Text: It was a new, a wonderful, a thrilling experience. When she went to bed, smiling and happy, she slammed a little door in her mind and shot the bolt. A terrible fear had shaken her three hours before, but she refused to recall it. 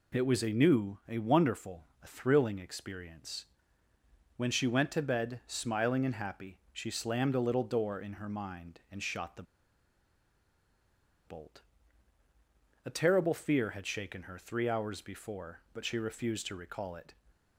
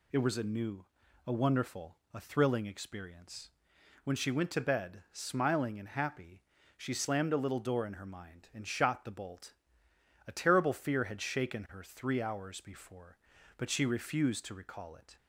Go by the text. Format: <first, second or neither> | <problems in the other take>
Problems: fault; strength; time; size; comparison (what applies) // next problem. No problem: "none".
second | pauses between "the" and "bolt"; strong; at 9.4 s; 1.8 s long